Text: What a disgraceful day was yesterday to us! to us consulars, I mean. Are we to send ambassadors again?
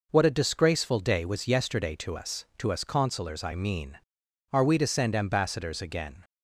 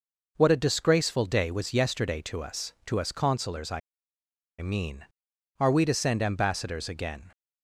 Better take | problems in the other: first | pauses between "I" and "mean"; noticeable; at 3.8 s; 0.81 s long

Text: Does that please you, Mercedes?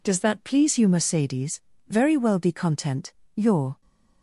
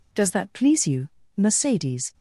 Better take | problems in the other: second | goes on to say "Very well be content your"; strong; from 1.8 s on; 1.9 s long

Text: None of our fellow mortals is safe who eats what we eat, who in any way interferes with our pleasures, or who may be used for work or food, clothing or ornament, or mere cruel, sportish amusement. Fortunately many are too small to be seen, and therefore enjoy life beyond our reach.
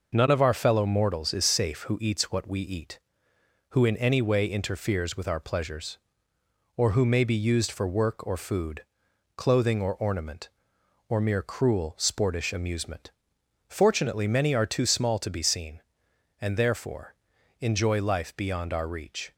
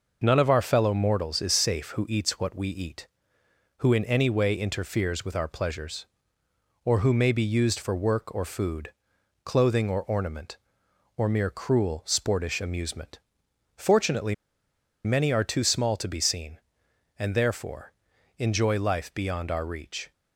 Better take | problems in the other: first | pauses between "Fortunately" and "many"; noticeable; at 14.3 s; 0.71 s long // pauses between "therefore" and "enjoy"; at 17.9 s; 0.44 s long; also in the first

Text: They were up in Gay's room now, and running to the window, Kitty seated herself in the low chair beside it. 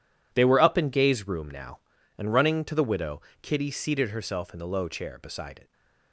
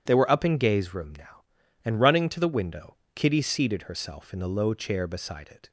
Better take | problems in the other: second | says "widow" for "window"; at 2.8 s // stays silent after the last word; slight; from 5.6 s on; 0.5 s long

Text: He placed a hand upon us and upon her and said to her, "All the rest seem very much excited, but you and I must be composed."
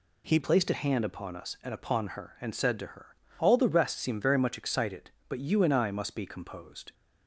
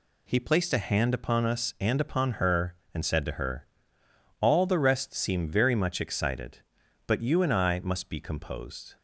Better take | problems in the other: second | changes voice at "placed"; from 0.4 s on; 6.5 s long

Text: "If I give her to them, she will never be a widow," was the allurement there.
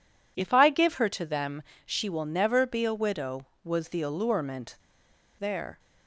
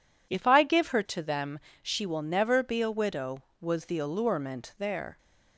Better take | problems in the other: second | pauses between "allurement" and "there"; noticeable; at 4.7 s; 0.63 s long

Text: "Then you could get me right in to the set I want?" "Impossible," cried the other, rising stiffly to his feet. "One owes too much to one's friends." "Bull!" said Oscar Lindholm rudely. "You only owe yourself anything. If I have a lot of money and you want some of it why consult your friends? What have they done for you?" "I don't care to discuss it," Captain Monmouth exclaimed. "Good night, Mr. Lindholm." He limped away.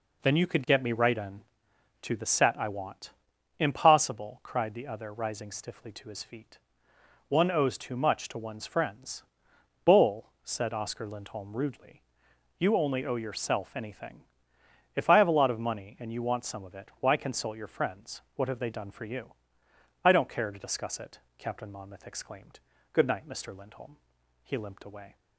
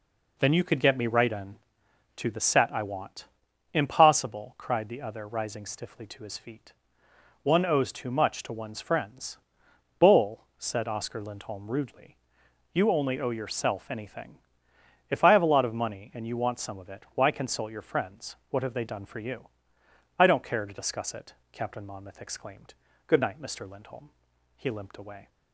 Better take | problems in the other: neither | none

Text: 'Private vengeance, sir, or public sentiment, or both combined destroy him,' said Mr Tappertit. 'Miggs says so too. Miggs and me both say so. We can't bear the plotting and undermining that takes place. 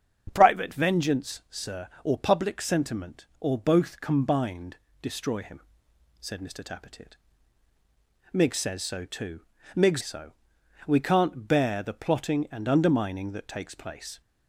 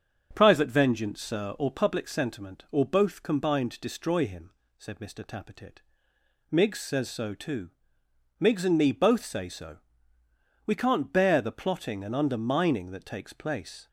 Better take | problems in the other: second | starts louder than the rest; strong; until 1.3 s; 7.5 dB; also in the second // pauses between "combined" and "destroy"; slight; at 4.7 s; 0.24 s long // skips "and me both say"; at 10.0 s

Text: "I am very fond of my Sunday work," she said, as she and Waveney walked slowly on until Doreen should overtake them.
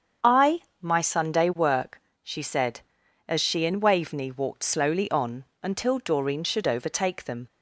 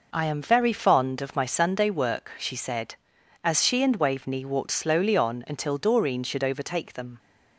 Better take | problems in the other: second | starts louder than the rest; strong; until 1.4 s; 7.5 dB // skips "am very fond of"; at 0.7 s // pauses between "on" and "until"; slight; at 5.4 s; 0.18 s long

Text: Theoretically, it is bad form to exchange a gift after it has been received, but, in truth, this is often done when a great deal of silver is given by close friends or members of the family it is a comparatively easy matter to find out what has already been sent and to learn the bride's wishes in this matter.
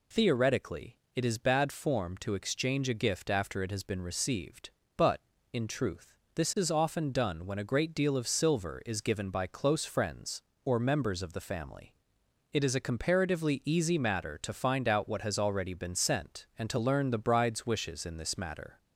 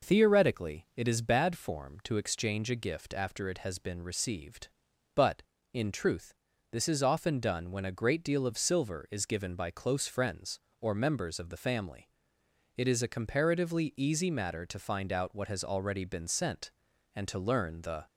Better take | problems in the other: first | pauses between "family" and "it"; noticeable; at 12.0 s; 0.66 s long; noticeable in the first // stops before "bride's wishes in this matter"; at 18.0 s

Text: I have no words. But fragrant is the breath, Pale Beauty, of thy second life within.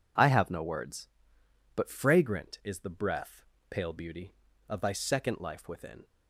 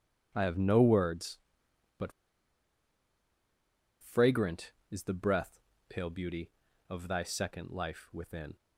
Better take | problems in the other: first | pauses between "But" and "fragrant"; strong; at 2.1 s; 1.8 s long

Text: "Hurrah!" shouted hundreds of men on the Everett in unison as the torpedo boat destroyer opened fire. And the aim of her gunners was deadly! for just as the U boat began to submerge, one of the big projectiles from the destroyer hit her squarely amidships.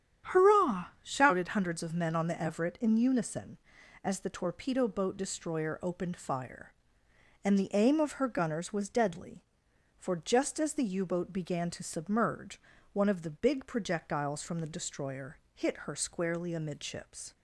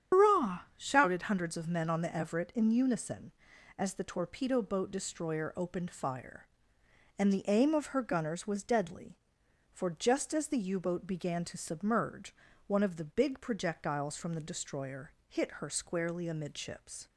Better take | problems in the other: first | loses the start of "Hurrah"; at 0.1 s; 135 ms // starts louder than the rest; strong; until 1.2 s; 8.5 dB; strong in the first // pauses between "destroyer" and "hit"; slight; at 15.1 s; 0.16 s long; slight in the first

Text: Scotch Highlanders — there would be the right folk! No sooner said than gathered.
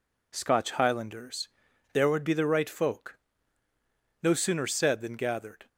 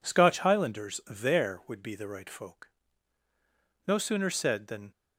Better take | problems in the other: first | stops before "gathered"; at 4.9 s

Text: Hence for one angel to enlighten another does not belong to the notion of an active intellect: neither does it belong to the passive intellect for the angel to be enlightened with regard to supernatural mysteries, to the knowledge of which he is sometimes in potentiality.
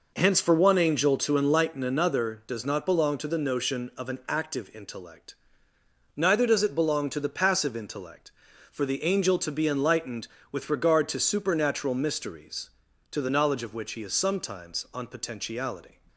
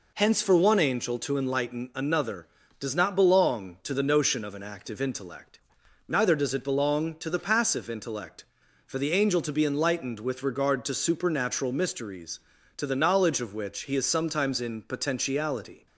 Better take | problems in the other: second | says "on" for "in"; at 14.9 s

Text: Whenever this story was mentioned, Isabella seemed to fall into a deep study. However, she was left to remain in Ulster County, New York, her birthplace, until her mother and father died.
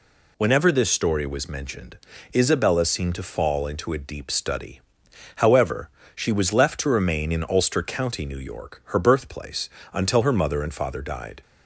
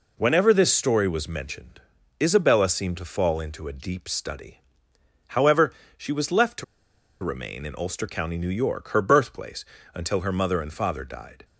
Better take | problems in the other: first | pauses between "to" and "remain"; noticeable; at 6.6 s; 0.58 s long

